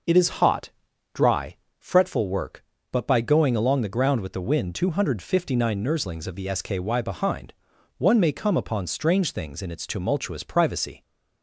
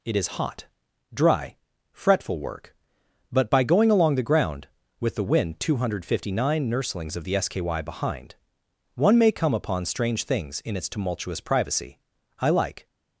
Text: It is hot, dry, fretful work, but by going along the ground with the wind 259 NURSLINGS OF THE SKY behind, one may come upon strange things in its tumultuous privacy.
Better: first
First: none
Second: goes on to say "I like"; slight; from 12.3 s on; 0.48 s long

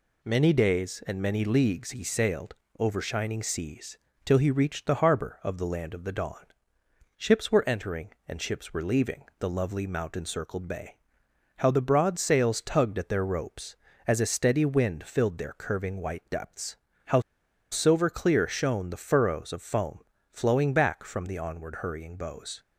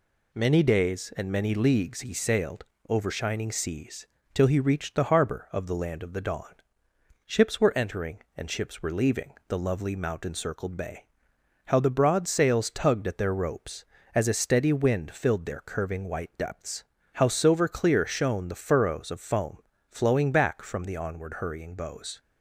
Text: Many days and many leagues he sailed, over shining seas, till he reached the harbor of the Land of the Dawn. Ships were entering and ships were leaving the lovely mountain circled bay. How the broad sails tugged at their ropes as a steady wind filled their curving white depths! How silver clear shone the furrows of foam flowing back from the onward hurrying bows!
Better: second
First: pauses between "leaving" and "the"; slight; at 9.2 s; 0.16 s long // pauses between "How" and "silver"; noticeable; at 17.2 s; 0.49 s long // pauses between "foam" and "flowing"; slight; at 20.0 s; 0.30 s long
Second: pauses between "leaving" and "the"; slight; at 9.3 s; 0.16 s long // pauses between "foam" and "flowing"; slight; at 19.5 s; 0.30 s long

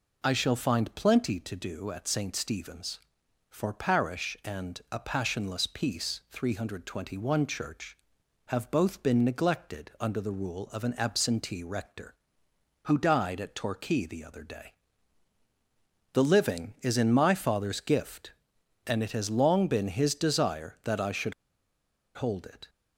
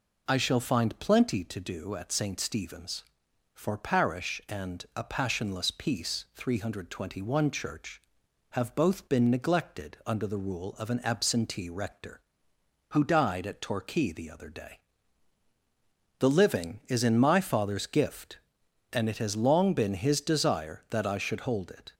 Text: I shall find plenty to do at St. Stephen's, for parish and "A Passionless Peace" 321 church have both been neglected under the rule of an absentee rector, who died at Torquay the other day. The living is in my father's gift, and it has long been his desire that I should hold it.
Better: second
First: pauses between "should" and "hold"; noticeable; at 21.3 s; 0.83 s long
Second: none

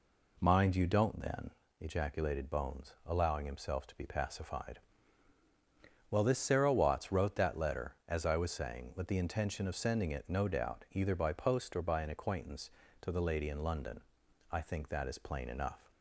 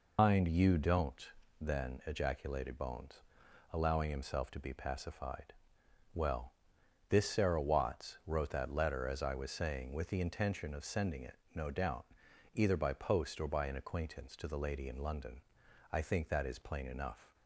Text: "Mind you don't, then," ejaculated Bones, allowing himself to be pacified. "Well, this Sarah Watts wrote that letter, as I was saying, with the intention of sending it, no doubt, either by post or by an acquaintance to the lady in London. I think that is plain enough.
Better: first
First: none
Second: loses the start of "Mind"; at 0.1 s; 135 ms

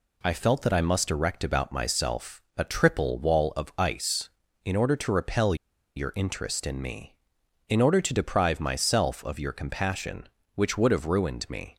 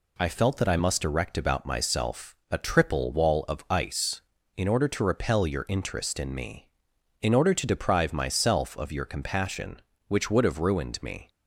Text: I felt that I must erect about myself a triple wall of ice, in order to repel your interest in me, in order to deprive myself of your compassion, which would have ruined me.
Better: second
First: pauses between "repel" and "your"; at 5.5 s; 0.41 s long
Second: none

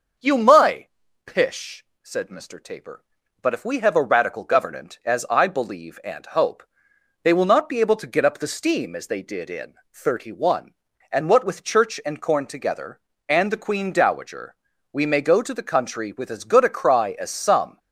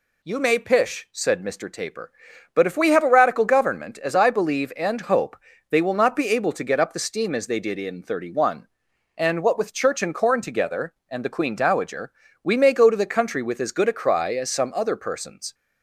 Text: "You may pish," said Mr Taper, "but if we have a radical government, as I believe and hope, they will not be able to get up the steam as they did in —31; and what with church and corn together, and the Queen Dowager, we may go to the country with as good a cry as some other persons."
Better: second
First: starts louder than the rest; noticeable; until 1.5 s; 6 dB // pauses between "may" and "pish"; at 0.8 s; 0.38 s long // stops before "other persons"; at 17.7 s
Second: none

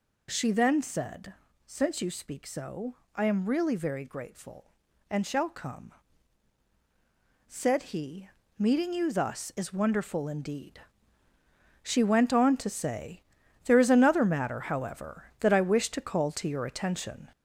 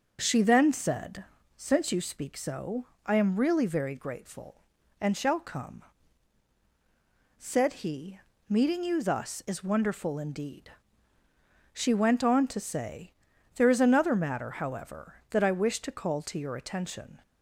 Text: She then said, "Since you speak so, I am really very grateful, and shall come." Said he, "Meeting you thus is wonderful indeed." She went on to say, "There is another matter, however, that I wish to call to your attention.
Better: second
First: gets louder; noticeable; throughout; 4.5 dB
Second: none

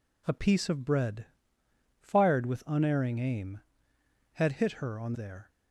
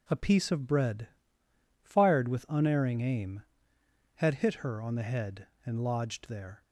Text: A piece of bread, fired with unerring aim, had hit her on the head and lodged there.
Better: second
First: skips "the head and lodged"; at 5.1 s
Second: none

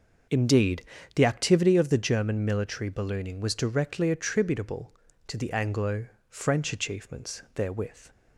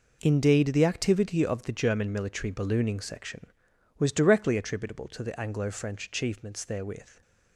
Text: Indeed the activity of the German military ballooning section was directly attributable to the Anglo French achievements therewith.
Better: second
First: starts louder than the rest; noticeable; until 1.6 s; 6 dB // pauses between "Indeed" and "the"; slight; at 0.8 s; 0.32 s long // skips "section"; at 3.3 s // pauses between "Anglo" and "French"; slight; at 6.0 s; 0.24 s long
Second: none

